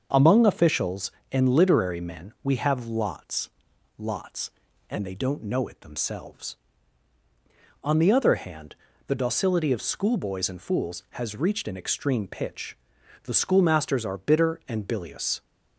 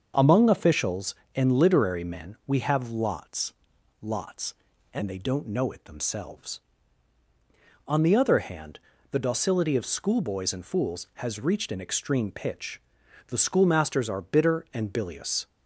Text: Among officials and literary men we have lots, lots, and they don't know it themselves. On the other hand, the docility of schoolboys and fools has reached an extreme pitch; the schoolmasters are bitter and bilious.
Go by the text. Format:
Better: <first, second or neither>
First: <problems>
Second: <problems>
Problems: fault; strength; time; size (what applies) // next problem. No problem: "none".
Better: neither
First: starts louder than the rest; until 1.3 s; 6.5 dB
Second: starts louder than the rest; until 1.3 s; 6.5 dB